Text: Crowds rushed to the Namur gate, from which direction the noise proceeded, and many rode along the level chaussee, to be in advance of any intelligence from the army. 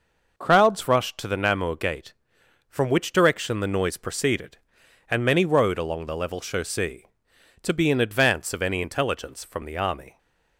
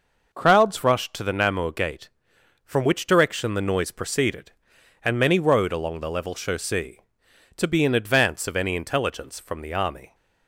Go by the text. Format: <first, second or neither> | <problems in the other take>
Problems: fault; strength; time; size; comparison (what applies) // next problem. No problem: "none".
neither | none